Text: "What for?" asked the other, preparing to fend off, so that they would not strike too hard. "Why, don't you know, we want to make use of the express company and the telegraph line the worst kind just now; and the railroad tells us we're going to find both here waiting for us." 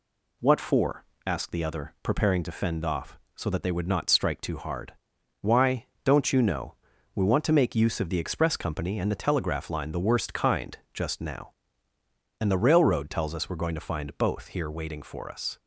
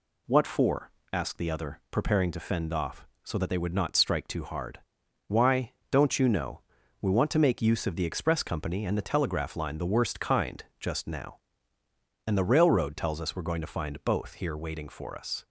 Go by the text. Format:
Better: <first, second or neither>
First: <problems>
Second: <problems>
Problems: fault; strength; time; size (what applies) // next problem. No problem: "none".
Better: neither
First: none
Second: none